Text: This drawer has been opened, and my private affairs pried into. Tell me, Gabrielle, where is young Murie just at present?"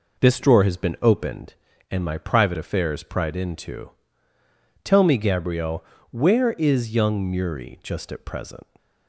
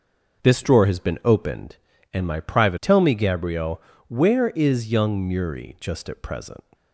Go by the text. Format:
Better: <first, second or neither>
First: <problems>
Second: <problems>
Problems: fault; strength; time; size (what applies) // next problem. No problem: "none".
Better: first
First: none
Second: skips "affairs pried into"; at 2.7 s